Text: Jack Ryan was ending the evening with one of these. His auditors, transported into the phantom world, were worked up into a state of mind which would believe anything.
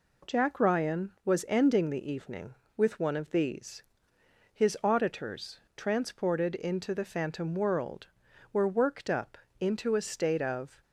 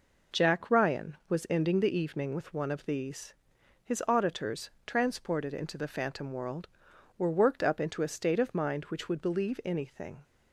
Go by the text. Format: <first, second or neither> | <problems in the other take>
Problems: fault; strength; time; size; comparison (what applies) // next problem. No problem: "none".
second | pauses between "up" and "into"; slight; at 9.3 s; 0.24 s long // stops before "mind which would believe anything"; at 10.8 s